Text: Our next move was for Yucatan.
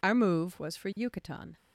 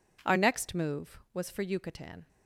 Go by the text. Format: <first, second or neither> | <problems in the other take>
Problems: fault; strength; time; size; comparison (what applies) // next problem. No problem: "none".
second | skips "next"; at 0.1 s